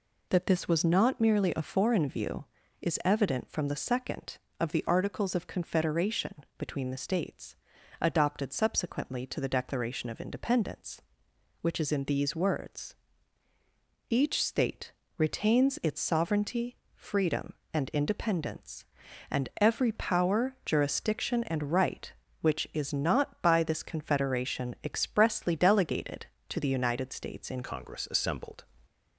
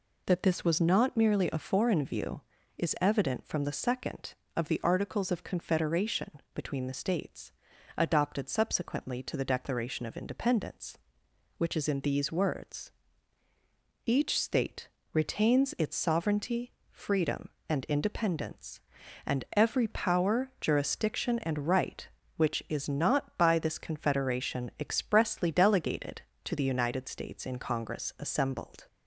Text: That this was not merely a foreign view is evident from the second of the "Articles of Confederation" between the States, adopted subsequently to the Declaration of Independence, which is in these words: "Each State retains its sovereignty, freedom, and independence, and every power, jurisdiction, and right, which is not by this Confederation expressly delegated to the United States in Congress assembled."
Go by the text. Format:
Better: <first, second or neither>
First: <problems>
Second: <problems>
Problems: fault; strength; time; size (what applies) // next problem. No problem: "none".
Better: second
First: pauses between "State" and "retains"; slight; at 14.9 s; 0.26 s long // changes voice at "Congress"; from 27.6 s on; 1.0 s long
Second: pauses between "State" and "retains"; slight; at 14.8 s; 0.25 s long